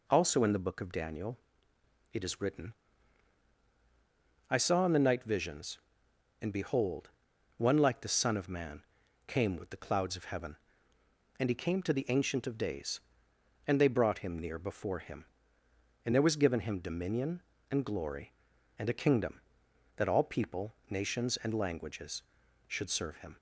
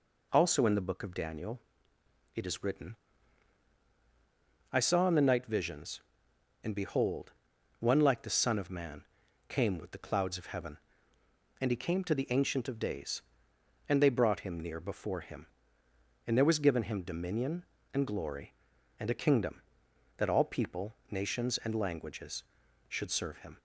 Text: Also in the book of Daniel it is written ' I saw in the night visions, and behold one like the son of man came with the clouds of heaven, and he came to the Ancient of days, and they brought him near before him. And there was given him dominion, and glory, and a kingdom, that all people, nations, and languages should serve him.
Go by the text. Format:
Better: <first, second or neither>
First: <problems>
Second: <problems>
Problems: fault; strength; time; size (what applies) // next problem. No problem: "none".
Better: neither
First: pauses between "Daniel" and "it"; noticeable; at 1.3 s; 0.76 s long // pauses between "behold" and "one"; noticeable; at 7.1 s; 0.46 s long // pauses between "man" and "came"; at 8.8 s; 0.42 s long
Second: pauses between "Daniel" and "it"; noticeable; at 1.5 s; 0.76 s long // pauses between "behold" and "one"; noticeable; at 7.3 s; 0.46 s long // pauses between "man" and "came"; at 9.0 s; 0.42 s long